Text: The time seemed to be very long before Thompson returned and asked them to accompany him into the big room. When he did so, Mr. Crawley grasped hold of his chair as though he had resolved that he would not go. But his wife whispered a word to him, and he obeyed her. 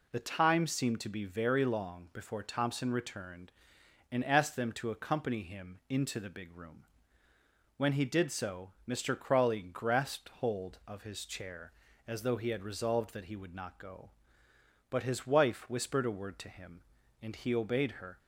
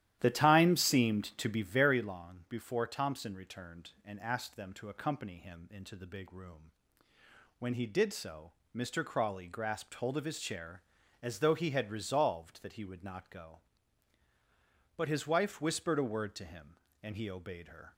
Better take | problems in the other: first | starts louder than the rest; strong; until 1.9 s; 12.5 dB

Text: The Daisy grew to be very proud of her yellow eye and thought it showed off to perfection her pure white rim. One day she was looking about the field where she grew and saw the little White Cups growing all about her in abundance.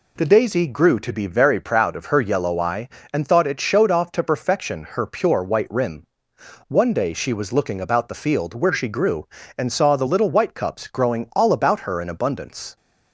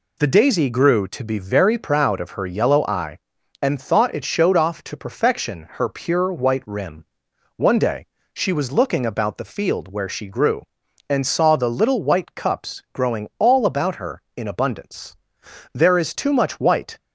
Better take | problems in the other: first | pauses between "day" and "she"; slight; at 8.0 s; 0.28 s long // goes on to say "There is too much white"; noticeable; from 15.7 s on; 1.2 s long

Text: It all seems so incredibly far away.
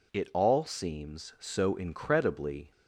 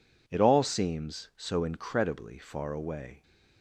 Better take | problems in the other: second | stops before "far away"; at 2.7 s

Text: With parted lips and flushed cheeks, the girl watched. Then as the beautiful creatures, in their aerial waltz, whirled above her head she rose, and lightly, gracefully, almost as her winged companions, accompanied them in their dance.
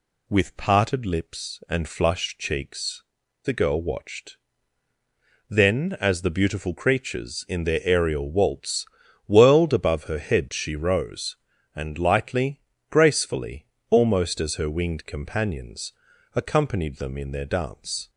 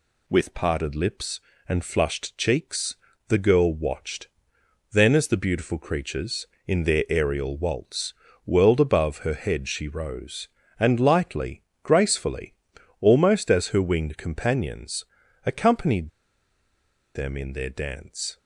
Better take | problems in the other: first | pauses between "accompanied" and "them"; at 16.0 s; 1.0 s long

